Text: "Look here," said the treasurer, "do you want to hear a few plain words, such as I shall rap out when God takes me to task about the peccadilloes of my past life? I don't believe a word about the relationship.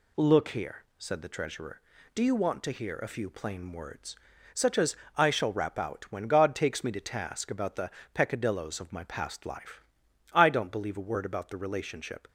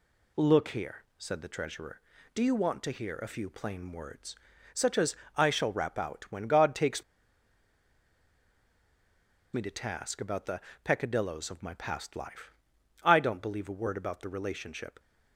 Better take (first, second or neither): first